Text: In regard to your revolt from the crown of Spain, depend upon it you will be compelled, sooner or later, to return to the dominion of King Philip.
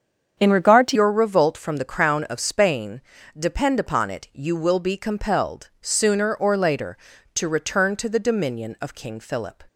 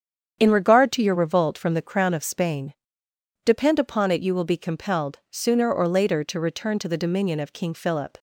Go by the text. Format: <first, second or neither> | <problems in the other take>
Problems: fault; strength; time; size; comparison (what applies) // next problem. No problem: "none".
second | starts louder than the rest; strong; until 1.4 s; 7.5 dB; strong in the second // changes voice at "your"; from 0.9 s on; 8.7 s long